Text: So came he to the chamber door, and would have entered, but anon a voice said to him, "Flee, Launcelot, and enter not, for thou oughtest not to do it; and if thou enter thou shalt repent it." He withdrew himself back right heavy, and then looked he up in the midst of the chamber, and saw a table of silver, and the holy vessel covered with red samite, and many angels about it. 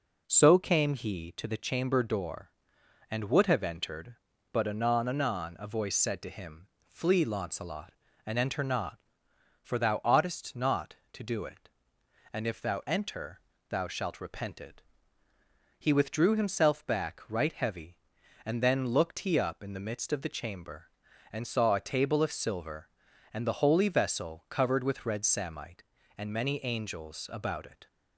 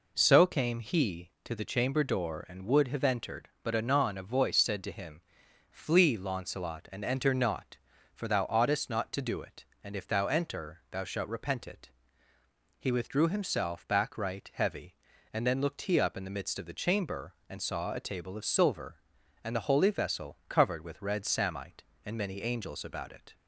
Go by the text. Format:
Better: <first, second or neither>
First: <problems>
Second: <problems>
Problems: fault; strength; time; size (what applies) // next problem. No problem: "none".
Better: second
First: says "anon" twice; at 5.0 s // pauses between "enter" and "thou"; slight; at 13.4 s; 0.28 s long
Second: none